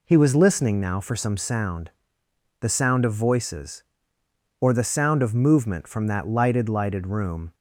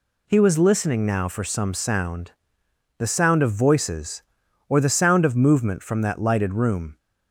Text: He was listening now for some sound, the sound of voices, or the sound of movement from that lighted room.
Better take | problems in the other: second | says "lighted" twice; at 6.6 s

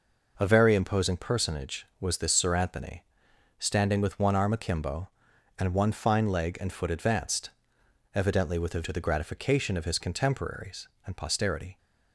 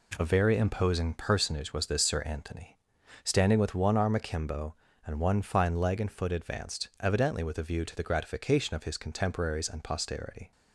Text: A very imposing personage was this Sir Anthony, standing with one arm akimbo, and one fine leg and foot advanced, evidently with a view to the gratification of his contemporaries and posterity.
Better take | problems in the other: second | skips "view"; at 8.8 s

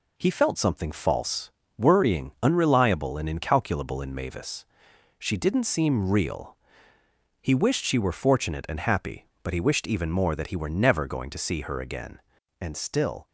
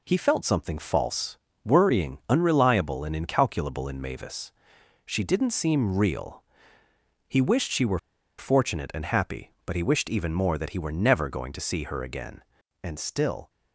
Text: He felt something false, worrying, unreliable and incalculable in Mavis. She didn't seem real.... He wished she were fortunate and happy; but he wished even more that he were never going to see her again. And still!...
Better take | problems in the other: first | pauses between "were" and "fortunate"; at 7.9 s; 0.41 s long

